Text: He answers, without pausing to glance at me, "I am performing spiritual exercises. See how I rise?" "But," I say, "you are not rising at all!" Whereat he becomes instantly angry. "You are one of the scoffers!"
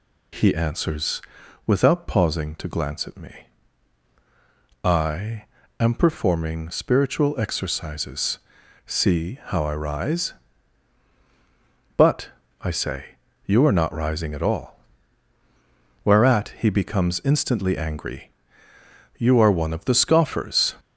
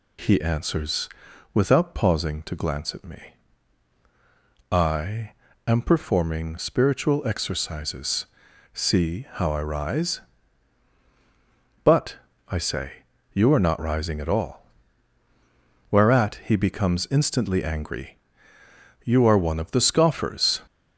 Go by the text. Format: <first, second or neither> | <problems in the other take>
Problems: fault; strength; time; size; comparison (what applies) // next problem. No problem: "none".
neither | pauses between "I" and "am"; slight; the same in both